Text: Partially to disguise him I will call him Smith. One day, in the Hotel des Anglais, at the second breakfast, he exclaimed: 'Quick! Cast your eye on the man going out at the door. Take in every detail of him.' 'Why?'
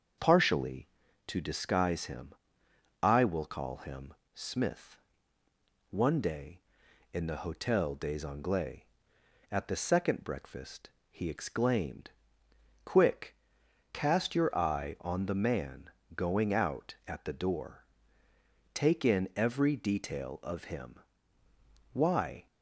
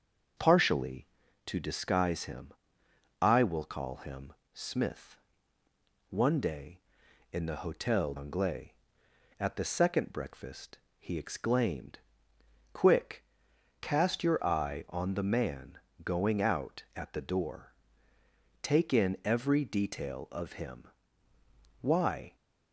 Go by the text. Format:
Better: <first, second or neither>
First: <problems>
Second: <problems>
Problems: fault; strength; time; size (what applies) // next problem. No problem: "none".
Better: first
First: starts louder than the rest; until 1.5 s; 6.5 dB // pauses between "him" and "I"; noticeable; at 2.3 s; 0.68 s long // pauses between "him" and "Smith"; slight; at 4.1 s; 0.22 s long // pauses between "man" and "going"; slight; at 15.8 s; 0.28 s long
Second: starts louder than the rest; until 1.7 s; 6.5 dB // pauses between "him" and "I"; noticeable; at 2.5 s; 0.68 s long // pauses between "him" and "Smith"; slight; at 4.3 s; 0.22 s long // skips "des"; at 8.1 s // pauses between "man" and "going"; slight; at 15.7 s; 0.28 s long